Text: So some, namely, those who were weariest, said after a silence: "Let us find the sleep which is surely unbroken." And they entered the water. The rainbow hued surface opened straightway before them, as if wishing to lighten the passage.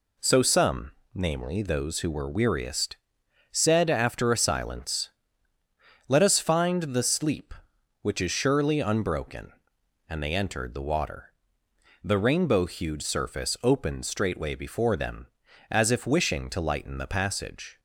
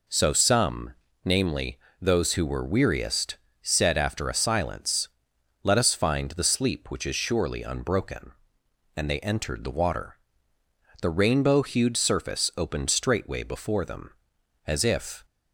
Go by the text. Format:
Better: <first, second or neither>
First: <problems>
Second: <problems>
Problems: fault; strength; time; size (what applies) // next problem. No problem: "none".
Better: first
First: none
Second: stops before "wishing to lighten the passage"; at 15.2 s